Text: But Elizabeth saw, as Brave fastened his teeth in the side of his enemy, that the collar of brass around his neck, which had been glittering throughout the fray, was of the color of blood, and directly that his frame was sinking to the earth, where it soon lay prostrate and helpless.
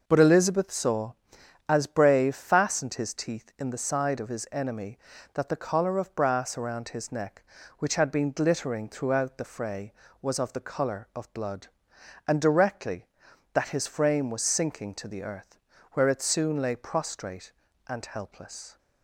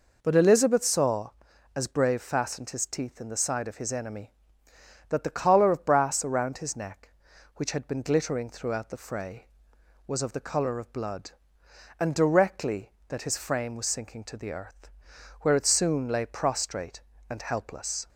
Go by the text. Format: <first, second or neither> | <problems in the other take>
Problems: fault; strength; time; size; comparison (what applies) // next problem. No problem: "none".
neither | none